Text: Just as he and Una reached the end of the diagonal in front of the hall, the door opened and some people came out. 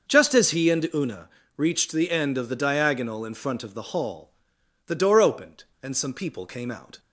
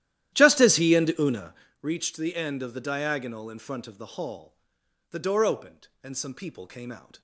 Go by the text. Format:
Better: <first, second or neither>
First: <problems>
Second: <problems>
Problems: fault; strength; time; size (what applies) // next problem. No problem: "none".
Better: first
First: pauses between "Una" and "reached"; slight; at 1.2 s; 0.28 s long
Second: starts louder than the rest; strong; until 1.8 s; 12.5 dB // pauses between "Una" and "reached"; slight; at 1.5 s; 0.28 s long